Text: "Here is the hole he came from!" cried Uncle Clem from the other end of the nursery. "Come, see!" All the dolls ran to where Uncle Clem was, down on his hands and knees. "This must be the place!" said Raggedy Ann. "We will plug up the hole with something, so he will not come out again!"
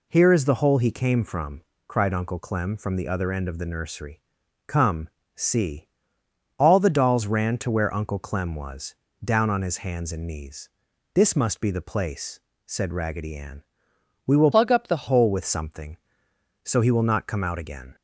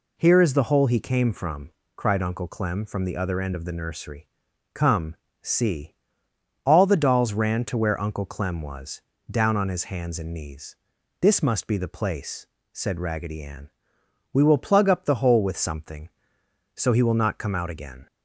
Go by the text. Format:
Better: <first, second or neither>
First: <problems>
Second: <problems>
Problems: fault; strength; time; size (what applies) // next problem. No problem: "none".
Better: second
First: changes voice from "plug" to "the"; from 14.5 to 15.0 s; 0.5 s long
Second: none